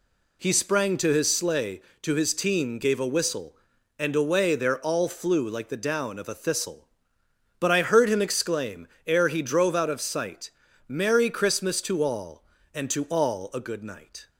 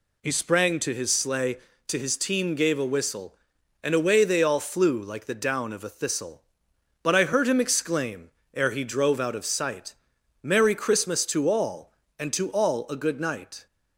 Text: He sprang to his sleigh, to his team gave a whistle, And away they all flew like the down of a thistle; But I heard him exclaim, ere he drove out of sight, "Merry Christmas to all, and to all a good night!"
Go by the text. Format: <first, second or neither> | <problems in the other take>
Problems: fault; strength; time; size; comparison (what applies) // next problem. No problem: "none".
second | says "there" for "they"; at 4.5 s